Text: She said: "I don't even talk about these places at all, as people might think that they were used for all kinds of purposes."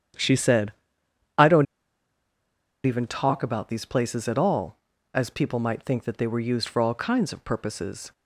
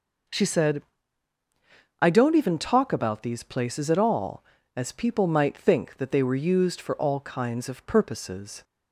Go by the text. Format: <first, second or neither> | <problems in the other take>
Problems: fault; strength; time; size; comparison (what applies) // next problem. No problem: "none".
second | starts louder than the rest; strong; until 3.0 s; 9 dB // pauses between "don't" and "even"; at 1.6 s; 1.2 s long